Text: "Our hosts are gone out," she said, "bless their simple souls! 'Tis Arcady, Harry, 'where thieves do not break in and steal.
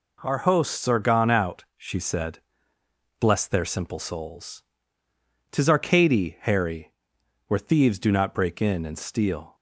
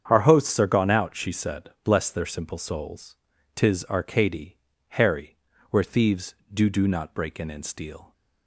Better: first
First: none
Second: starts louder than the rest; strong; until 1.1 s; 7.5 dB // says "do" twice; at 6.7 s

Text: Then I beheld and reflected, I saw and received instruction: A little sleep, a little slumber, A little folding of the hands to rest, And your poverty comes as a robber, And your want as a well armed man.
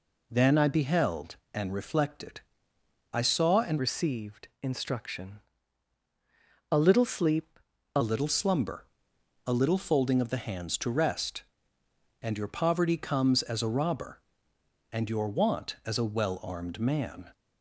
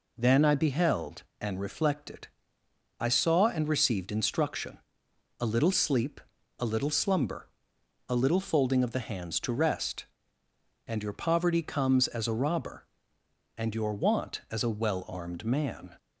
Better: second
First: changes voice from "received" to "a"; from 3.7 to 8.0 s; 4.3 s long // pauses between "received" and "instruction"; slight; at 4.4 s; 0.16 s long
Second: none

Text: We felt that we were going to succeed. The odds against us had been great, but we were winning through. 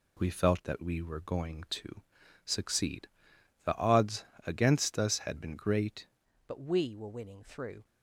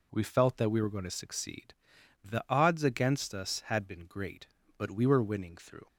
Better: second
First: pauses between "to" and "succeed"; at 2.0 s; 0.42 s long // pauses between "odds" and "against"; slight; at 4.2 s; 0.22 s long // changes voice at "but"; from 6.4 s on; 1.4 s long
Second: none

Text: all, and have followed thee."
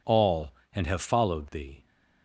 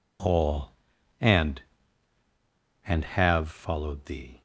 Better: first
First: none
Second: says "and" twice; at 2.8 s

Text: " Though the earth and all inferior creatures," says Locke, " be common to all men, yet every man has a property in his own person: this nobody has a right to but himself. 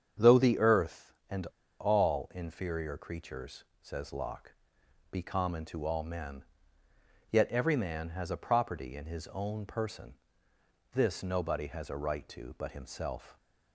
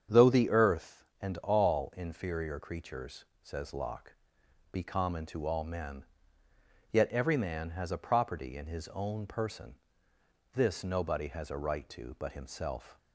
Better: second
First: starts louder than the rest; strong; until 1.3 s; 8 dB // pauses between "and" and "all"; slight; at 1.4 s; 0.34 s long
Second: starts louder than the rest; strong; until 1.2 s; 8 dB

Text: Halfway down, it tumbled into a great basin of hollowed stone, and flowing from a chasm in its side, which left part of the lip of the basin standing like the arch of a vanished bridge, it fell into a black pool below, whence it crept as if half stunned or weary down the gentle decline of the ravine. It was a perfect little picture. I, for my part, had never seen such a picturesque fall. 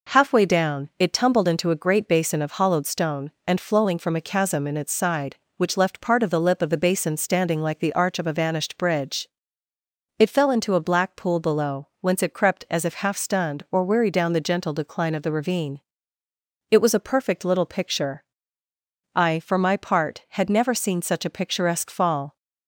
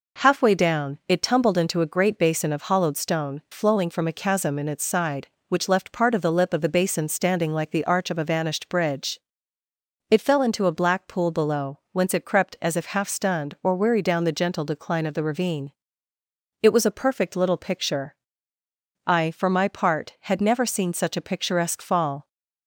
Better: first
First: none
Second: skips "and"; at 3.4 s

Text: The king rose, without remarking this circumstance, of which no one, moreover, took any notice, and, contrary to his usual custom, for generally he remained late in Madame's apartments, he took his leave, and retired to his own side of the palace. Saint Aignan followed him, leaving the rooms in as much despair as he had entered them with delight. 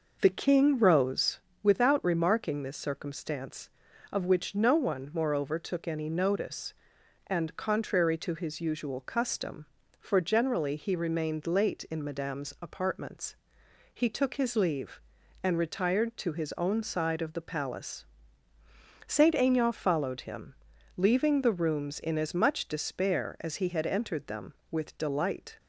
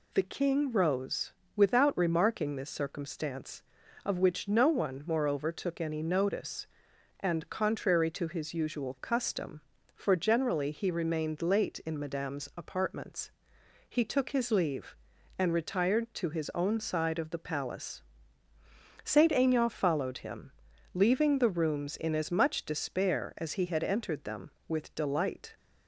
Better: second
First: starts louder than the rest; noticeable; until 1.4 s; 5.5 dB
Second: none

